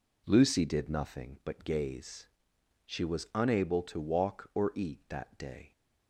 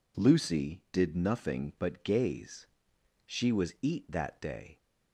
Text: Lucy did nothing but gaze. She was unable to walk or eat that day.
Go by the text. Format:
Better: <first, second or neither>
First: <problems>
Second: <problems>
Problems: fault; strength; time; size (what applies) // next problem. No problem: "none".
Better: first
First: none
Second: skips "unable to walk or"; at 3.7 s